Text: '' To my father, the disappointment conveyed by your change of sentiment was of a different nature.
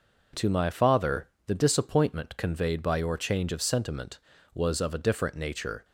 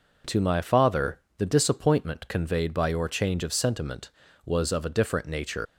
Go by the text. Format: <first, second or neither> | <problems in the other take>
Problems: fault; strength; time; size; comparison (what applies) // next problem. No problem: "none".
first | leaves "nature" unfinished; at 5.6 s; 100 ms